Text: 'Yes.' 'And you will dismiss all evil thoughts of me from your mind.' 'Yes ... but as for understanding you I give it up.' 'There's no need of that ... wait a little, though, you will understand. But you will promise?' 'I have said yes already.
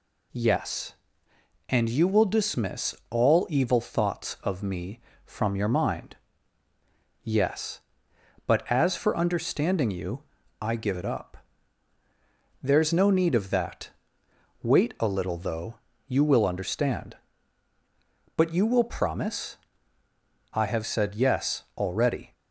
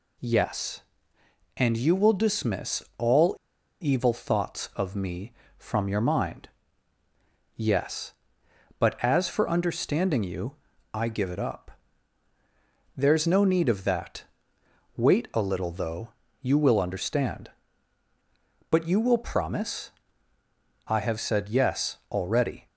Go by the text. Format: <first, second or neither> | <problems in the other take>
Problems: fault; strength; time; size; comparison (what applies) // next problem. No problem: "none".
first | pauses between "all" and "evil"; noticeable; at 3.3 s; 0.46 s long // pauses between "you" and "I"; at 10.5 s; 0.40 s long; also in the first